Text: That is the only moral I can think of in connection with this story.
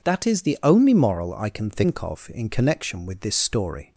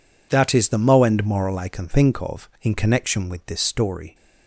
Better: first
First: none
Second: says "moend" for "only"; at 0.7 s

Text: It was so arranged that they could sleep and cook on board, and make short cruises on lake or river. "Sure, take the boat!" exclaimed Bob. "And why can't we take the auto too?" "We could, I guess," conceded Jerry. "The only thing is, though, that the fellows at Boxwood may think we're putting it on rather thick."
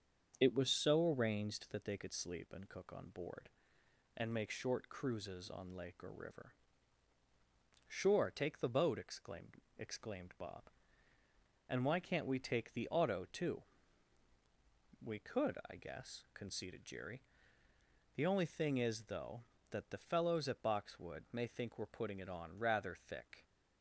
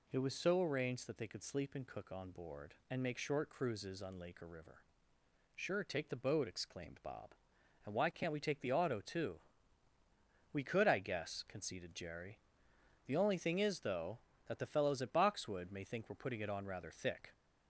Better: second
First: starts louder than the rest; until 1.4 s; 7 dB // says "exclaimed" twice; at 9.7 s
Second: none

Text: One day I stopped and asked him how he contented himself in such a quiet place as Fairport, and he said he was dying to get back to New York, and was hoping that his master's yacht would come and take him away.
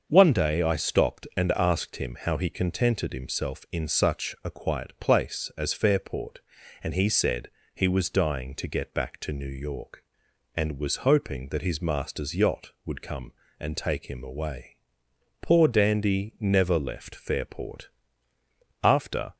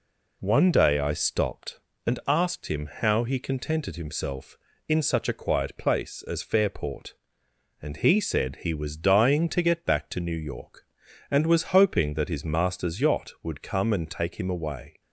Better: second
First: starts louder than the rest; until 1.1 s; 6.5 dB // pauses between "said" and "he"; slight; at 7.4 s; 0.24 s long // goes on to say "Poor Dandy never left Fairport After"; strong; from 15.4 s on; 3.9 s long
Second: none

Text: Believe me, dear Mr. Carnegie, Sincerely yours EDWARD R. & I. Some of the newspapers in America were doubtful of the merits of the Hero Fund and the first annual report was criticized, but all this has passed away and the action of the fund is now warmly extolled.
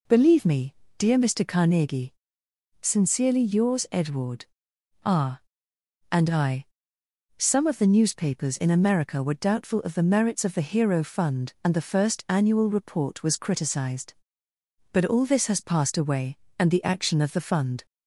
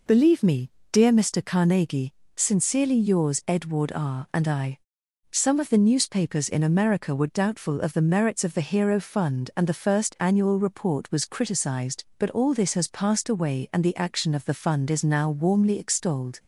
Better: second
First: pauses between "EDWARD" and "R"; noticeable; at 4.4 s; 0.58 s long // stops before "is now warmly extolled"; at 17.8 s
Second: none

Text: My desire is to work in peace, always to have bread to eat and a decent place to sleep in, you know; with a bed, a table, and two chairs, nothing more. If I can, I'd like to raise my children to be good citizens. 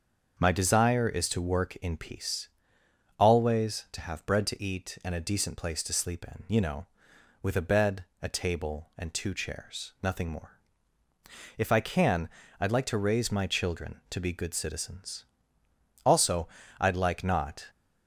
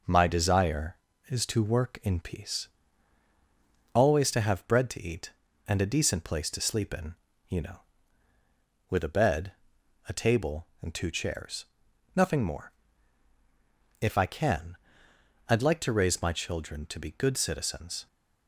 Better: second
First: starts louder than the rest; until 1.4 s; 6.5 dB // goes on to say "Also I'd like not"; from 16.0 s on; 1.6 s long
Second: none

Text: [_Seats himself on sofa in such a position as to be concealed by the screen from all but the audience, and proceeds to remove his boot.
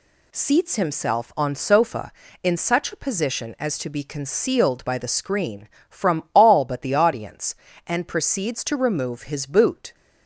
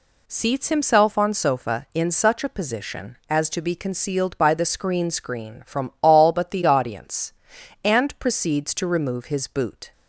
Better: first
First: none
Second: says "screen" twice; at 5.1 s

